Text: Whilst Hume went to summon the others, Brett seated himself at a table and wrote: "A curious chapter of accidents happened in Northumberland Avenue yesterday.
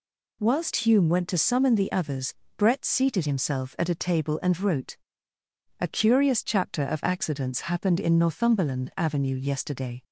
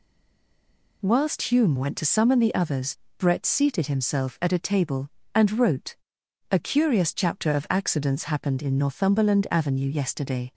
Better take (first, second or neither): first